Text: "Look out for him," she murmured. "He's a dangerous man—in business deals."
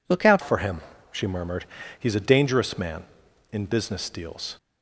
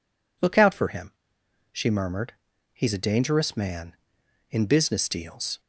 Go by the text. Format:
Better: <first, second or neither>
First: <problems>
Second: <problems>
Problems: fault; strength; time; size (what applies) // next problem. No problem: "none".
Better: second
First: changes voice at "for"; from 0.4 s on; 4.1 s long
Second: none